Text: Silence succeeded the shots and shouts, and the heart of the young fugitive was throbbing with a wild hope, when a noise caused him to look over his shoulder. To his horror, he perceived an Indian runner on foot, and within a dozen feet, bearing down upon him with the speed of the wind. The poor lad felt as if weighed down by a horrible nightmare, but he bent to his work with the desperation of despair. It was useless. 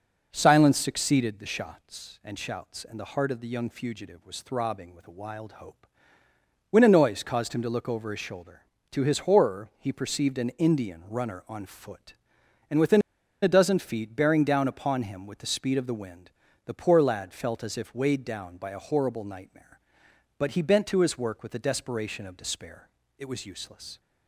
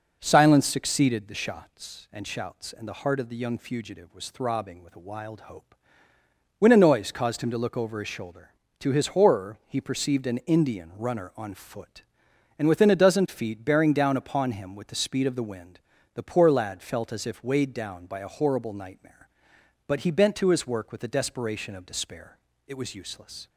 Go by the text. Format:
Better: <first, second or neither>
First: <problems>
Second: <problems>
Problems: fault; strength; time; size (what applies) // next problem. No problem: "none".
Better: second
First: pauses between "within" and "a"; at 13.0 s; 0.41 s long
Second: none